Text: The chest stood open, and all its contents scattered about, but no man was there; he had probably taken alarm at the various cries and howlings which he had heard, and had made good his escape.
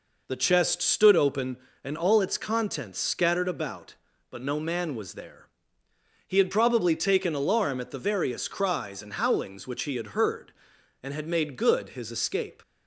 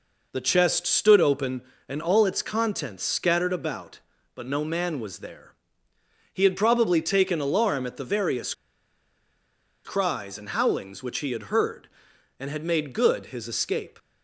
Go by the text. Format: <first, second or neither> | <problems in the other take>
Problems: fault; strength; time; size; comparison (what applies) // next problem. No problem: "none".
first | pauses between "various" and "cries"; strong; at 8.5 s; 1.3 s long